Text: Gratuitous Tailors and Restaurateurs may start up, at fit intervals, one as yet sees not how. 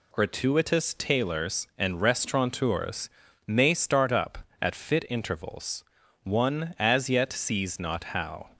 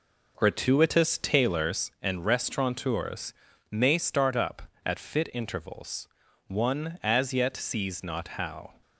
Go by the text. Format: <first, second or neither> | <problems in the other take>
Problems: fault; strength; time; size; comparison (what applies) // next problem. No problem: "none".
first | starts louder than the rest; noticeable; until 1.9 s; 5 dB // pauses between "Restaurateurs" and "may"; at 3.3 s; 0.38 s long; also in the first